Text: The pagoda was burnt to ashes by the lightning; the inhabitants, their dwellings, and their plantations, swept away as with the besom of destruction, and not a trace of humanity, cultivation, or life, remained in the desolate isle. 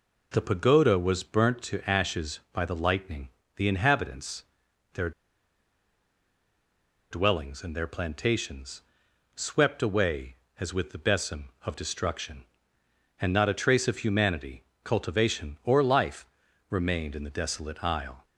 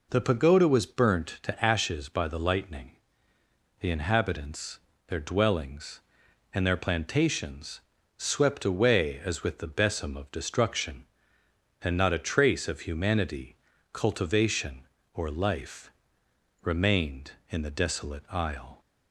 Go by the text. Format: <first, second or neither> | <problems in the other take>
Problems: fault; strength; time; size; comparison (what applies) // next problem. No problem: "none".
second | pauses between "their" and "dwellings"; strong; at 5.1 s; 2.0 s long